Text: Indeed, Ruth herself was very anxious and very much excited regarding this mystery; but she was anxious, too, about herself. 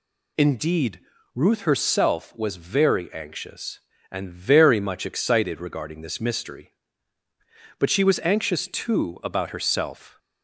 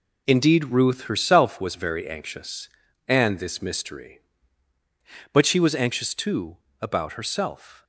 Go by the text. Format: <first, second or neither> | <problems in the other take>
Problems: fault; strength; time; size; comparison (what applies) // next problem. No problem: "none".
first | skips "very much excited regarding"; at 3.3 s